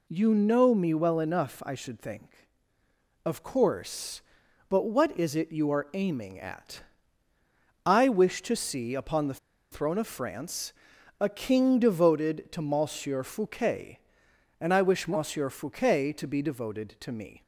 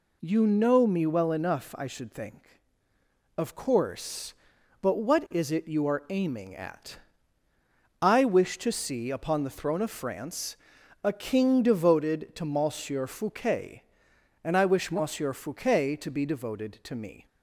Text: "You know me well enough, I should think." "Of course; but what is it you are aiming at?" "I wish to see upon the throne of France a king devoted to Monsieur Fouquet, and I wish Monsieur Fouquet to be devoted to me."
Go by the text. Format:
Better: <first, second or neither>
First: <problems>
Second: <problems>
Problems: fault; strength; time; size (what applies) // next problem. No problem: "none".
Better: second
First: pauses between "the" and "throne"; slight; at 9.3 s; 0.33 s long // pauses between "France" and "a"; noticeable; at 10.7 s; 0.48 s long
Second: pauses between "France" and "a"; noticeable; at 10.5 s; 0.48 s long